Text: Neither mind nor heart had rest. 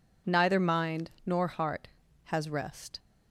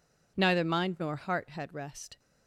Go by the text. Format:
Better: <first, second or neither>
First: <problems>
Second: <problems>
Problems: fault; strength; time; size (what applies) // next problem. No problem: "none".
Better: second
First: says "has" for "had"; at 2.2 s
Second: none